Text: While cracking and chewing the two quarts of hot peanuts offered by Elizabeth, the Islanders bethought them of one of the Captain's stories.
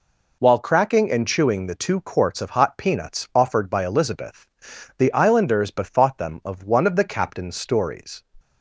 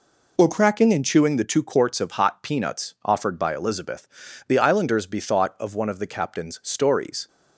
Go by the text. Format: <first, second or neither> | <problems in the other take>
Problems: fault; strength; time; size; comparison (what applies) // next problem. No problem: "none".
first | skips "them"; at 5.5 s